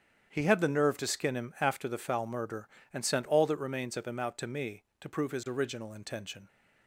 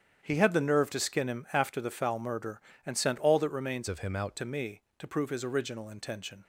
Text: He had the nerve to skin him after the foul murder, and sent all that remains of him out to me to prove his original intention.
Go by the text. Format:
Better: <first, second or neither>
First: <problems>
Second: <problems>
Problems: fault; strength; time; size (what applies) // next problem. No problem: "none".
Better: first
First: starts louder than the rest; strong; until 1.3 s; 8.5 dB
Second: starts louder than the rest; strong; until 1.2 s; 8.5 dB // changes voice from "of" to "out"; from 3.8 to 4.3 s; 0.5 s long